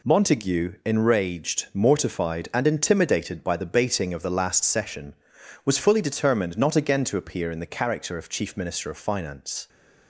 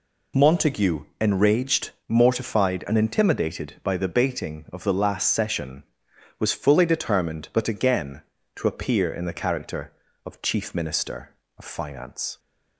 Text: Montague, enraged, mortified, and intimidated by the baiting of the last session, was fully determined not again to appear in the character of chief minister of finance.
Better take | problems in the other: first | says "but" for "not"; at 7.5 s

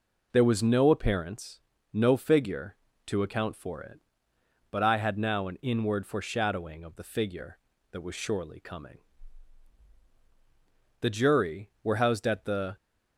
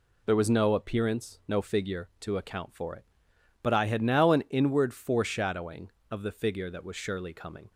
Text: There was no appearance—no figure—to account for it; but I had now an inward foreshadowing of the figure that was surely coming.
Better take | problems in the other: second | goes on to say "The Jury were housed at the"; strong; from 11.0 s on; 1.7 s long

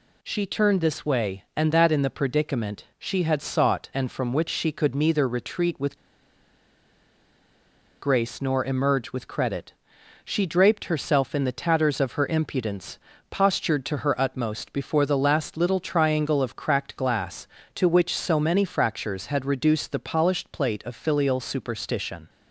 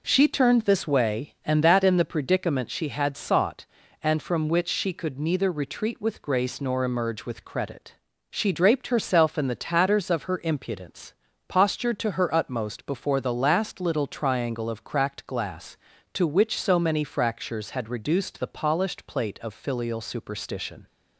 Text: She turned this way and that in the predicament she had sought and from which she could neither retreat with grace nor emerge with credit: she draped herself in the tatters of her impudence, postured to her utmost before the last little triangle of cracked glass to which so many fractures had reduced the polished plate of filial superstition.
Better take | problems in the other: second | pauses between "with" and "grace"; strong; at 5.9 s; 2.0 s long

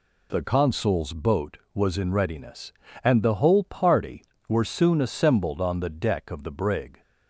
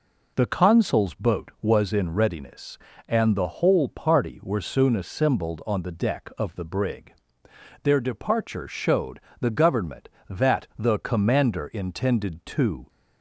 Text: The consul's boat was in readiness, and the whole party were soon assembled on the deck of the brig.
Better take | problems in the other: first | goes on to say "Their departure showed the government that the commander intended to"; strong; from 7.8 s on; 5.0 s long

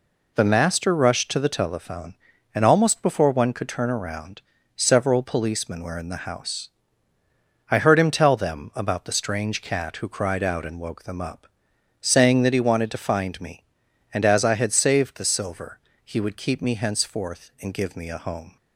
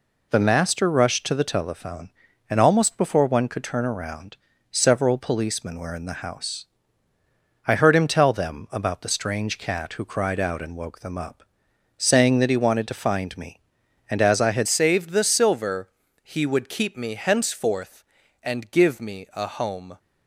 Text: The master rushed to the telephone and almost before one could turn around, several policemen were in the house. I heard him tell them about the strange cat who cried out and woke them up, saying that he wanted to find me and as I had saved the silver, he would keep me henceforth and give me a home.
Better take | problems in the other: first | changes voice at "saved"; from 14.6 s on; 5.3 s long

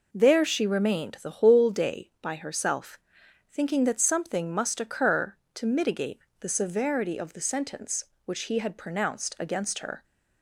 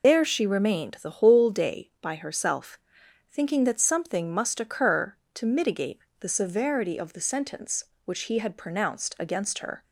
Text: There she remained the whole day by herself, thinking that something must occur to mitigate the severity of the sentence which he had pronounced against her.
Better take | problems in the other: first | loses the start of "There"; at 0.0 s; 120 ms // pauses between "mitigate" and "the"; slight; at 5.9 s; 0.20 s long; slight in the first

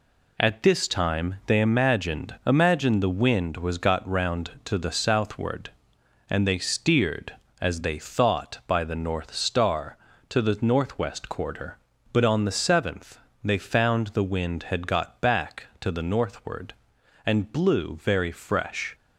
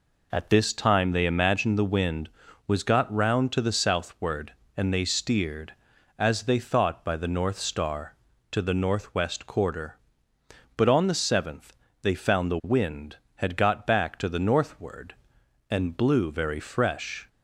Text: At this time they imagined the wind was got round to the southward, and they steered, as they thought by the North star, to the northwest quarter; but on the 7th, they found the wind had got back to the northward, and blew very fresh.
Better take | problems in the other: second | says "imagined" twice; at 2.4 s

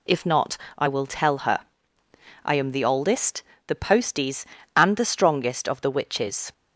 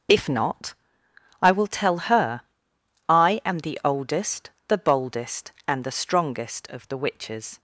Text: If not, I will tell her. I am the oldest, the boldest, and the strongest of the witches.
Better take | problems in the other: second | says "posties" for "boldest"; at 3.7 s

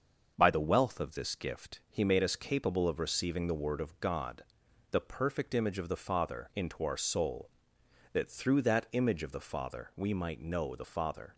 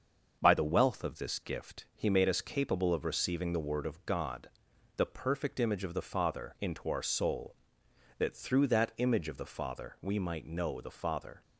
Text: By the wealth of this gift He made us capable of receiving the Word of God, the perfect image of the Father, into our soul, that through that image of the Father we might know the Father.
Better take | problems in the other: neither | starts louder than the rest; the same in both

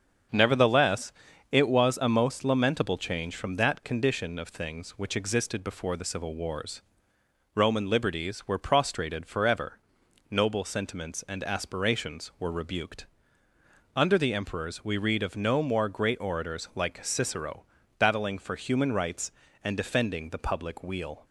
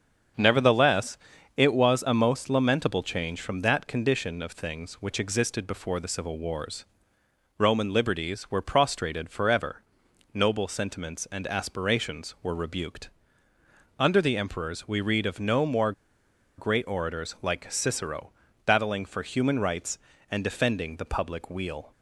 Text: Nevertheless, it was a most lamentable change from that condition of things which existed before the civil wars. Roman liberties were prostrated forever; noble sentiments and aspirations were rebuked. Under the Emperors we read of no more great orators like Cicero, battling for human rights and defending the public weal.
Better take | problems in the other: first | starts louder than the rest; strong; until 1.7 s; 7.5 dB; strong in the first // pauses between "more" and "great"; noticeable; at 15.9 s; 0.65 s long

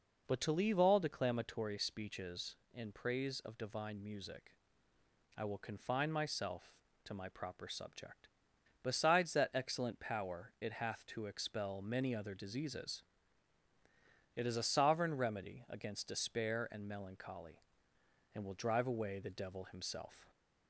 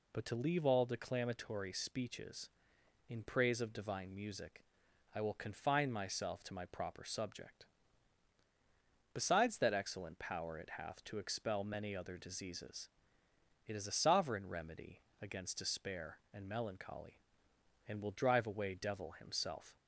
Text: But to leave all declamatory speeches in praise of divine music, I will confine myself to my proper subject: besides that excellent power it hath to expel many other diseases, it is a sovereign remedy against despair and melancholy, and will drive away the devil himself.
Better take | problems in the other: first | pauses between "remedy" and "against"; slight; at 14.9 s; 0.22 s long // skips "the"; at 18.7 s

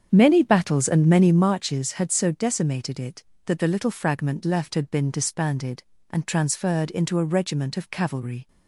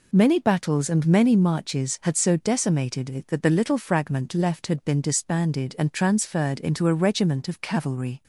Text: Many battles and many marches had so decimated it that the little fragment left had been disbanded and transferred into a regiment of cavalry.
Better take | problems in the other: second | starts louder than the rest; strong; until 1.6 s; 8 dB

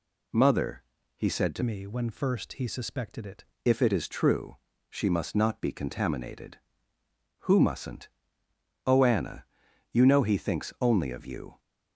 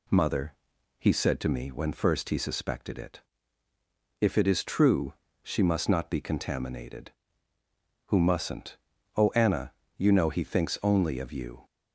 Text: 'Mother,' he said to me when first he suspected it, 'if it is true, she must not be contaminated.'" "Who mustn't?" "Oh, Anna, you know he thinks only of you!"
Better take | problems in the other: second | changes voice from "me" to "it"; from 1.6 to 3.4 s; 1.8 s long

